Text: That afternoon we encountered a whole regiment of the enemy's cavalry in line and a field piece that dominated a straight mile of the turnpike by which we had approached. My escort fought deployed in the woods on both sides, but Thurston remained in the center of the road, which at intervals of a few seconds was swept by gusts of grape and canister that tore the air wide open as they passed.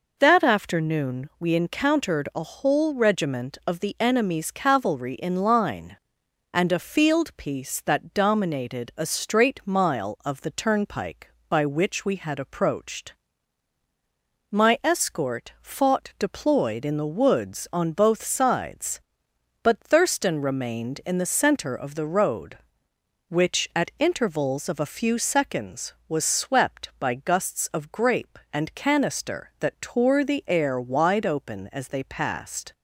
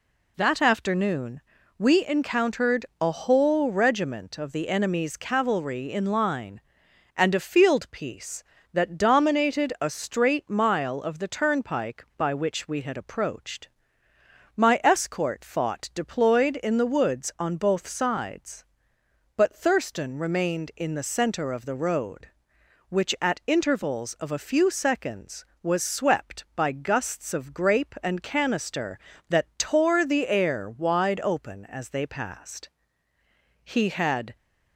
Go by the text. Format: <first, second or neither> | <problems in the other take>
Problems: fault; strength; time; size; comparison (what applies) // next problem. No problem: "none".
first | pauses between "afternoon" and "we"; at 1.4 s; 0.38 s long // pauses between "encountered" and "a"; slight; at 2.8 s; 0.16 s long // goes on to say "He had"; noticeable; from 33.6 s on; 0.72 s long